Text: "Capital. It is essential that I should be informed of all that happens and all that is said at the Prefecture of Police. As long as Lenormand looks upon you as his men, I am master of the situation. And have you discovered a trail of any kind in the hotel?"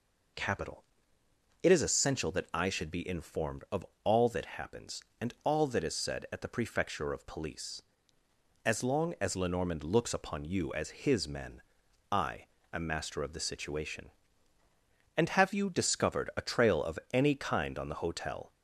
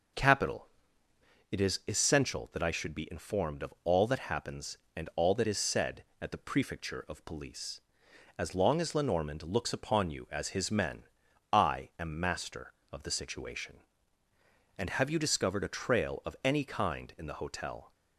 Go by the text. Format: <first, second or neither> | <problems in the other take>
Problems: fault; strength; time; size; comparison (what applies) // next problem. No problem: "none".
second | pauses between "of" and "all"; slight; at 3.8 s; 0.20 s long // pauses between "I" and "am"; slight; at 12.4 s; 0.24 s long // says "on" for "in"; at 17.7 s